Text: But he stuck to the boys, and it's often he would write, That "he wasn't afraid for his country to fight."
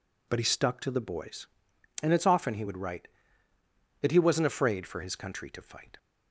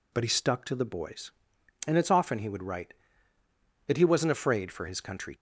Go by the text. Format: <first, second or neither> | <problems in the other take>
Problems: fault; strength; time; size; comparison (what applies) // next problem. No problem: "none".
first | stops before "to fight"; at 5.3 s